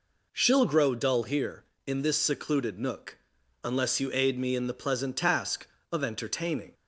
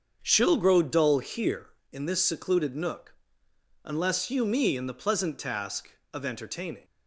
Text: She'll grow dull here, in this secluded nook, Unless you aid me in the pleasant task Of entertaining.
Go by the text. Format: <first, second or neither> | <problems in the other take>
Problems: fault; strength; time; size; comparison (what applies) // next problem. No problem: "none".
first | starts louder than the rest; until 1.2 s; 7 dB // skips "aid"; at 4.4 s